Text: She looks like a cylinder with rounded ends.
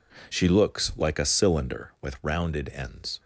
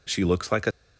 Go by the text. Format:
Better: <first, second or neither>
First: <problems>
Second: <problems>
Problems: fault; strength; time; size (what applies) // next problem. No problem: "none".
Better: first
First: none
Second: stops before "cylinder with rounded ends"; at 0.7 s